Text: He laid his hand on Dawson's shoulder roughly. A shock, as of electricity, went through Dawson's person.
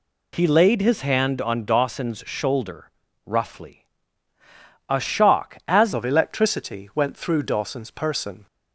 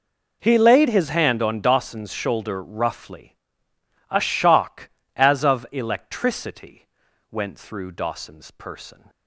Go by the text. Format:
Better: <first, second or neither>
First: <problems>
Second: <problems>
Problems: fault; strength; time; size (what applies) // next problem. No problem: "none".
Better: second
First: pauses between "shoulder" and "roughly"; slight; at 2.9 s; 0.34 s long // changes voice at "of"; from 5.9 s on; 2.5 s long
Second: none